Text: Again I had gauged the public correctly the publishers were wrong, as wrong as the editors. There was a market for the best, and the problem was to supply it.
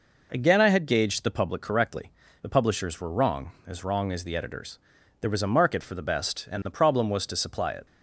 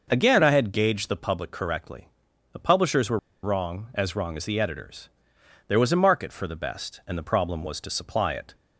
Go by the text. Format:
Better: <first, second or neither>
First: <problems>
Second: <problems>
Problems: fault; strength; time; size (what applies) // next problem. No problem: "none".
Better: first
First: pauses between "correctly" and "the"; slight; at 2.1 s; 0.32 s long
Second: pauses between "correctly" and "the"; at 2.0 s; 0.44 s long // pauses between "were" and "wrong"; slight; at 3.1 s; 0.24 s long